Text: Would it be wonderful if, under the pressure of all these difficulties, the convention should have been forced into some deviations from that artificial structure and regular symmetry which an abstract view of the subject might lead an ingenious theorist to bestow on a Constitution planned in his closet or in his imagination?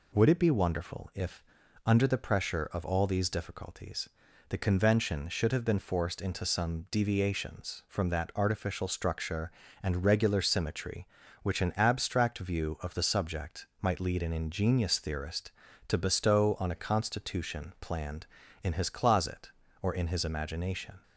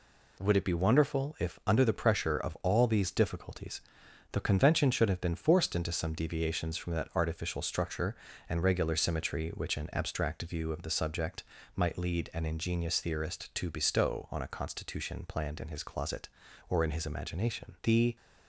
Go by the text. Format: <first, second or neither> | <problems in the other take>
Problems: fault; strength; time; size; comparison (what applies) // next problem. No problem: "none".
first | pauses between "subject" and "might"; slight; at 11.4 s; 0.32 s long; slight in the first // goes on to say "The"; slight; from 17.8 s on; 0.32 s long